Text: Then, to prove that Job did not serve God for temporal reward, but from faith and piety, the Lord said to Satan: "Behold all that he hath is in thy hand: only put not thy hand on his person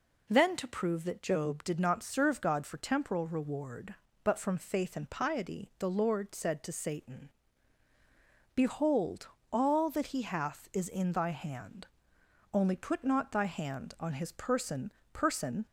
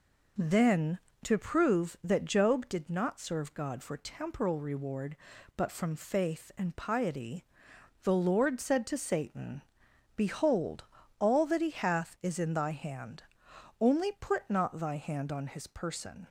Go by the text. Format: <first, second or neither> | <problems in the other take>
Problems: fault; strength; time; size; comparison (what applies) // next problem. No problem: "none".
second | pauses between "Behold" and "all"; slight; at 9.2 s; 0.24 s long; slight in the second // says "person" twice; at 15.1 s